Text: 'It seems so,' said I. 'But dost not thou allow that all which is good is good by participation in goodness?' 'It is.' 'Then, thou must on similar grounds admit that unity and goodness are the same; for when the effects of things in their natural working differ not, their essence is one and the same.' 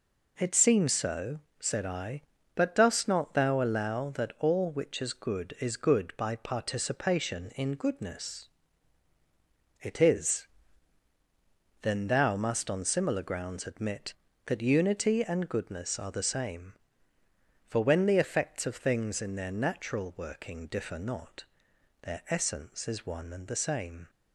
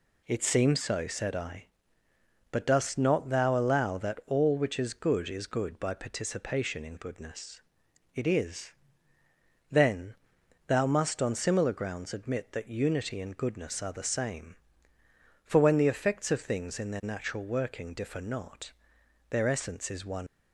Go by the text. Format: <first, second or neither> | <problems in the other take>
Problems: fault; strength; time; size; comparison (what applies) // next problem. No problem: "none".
first | stops before "and the same"; at 20.2 s